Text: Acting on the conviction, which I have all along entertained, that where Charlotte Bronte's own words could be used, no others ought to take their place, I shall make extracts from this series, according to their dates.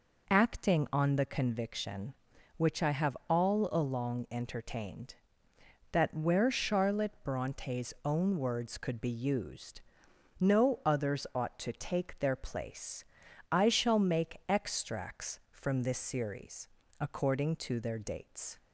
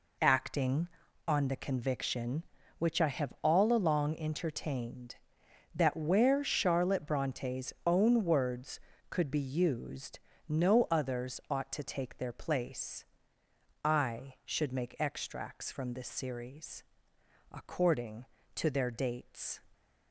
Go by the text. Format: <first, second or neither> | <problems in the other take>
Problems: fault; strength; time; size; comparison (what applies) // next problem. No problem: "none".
first | says "should" for "shall"; at 14.4 s